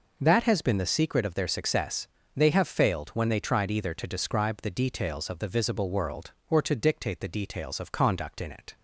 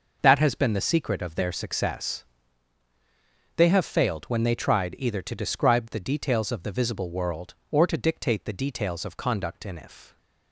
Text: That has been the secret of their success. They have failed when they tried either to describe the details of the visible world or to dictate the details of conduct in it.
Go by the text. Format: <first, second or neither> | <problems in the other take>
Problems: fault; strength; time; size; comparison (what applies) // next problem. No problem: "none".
first | says "if" for "it"; at 9.7 s